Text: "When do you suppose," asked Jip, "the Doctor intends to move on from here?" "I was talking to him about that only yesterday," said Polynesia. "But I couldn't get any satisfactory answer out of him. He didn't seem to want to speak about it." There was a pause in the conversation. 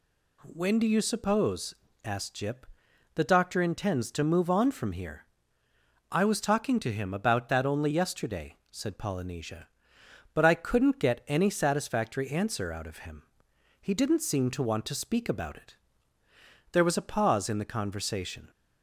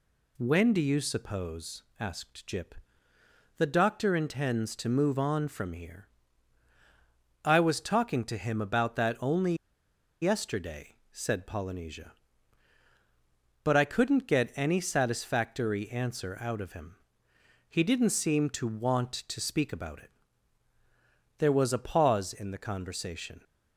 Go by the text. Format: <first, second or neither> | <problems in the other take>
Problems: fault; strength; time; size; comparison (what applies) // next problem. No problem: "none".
first | pauses between "only" and "yesterday"; noticeable; at 9.5 s; 0.67 s long